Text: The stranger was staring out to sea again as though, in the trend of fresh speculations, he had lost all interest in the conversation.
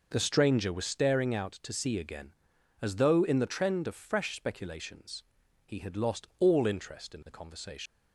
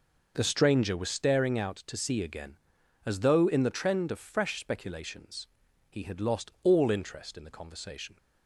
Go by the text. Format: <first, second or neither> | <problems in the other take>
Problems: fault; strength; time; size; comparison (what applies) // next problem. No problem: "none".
second | leaves "conversation" unfinished; at 7.8 s; 115 ms